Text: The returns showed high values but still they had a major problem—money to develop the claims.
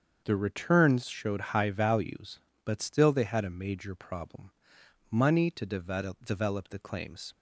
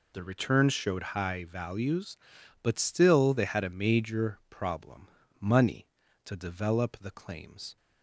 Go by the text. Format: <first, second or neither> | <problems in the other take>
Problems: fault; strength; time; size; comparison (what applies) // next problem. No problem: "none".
second | starts louder than the rest; until 1.2 s; 6.5 dB // says "develop" twice; at 6.2 s